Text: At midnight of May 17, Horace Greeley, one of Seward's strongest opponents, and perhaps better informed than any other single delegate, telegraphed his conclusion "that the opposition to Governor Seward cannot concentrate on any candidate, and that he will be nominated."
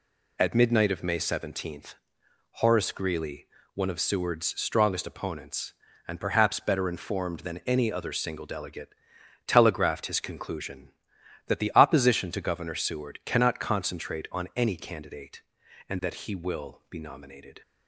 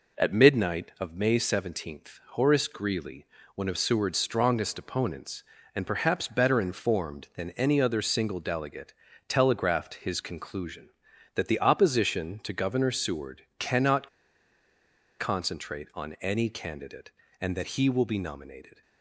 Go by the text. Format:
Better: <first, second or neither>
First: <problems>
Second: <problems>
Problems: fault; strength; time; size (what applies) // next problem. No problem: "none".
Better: first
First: none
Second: pauses between "Seward" and "cannot"; slight; at 13.4 s; 0.16 s long // pauses between "cannot" and "concentrate"; at 14.0 s; 1.1 s long